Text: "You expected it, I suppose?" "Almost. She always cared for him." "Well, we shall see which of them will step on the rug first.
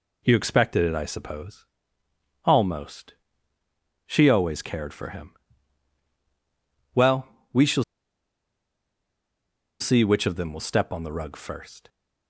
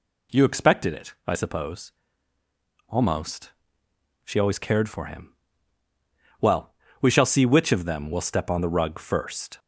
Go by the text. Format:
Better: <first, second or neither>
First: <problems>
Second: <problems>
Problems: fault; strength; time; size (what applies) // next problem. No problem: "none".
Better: second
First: pauses between "shall" and "see"; strong; at 7.8 s; 1.9 s long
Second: none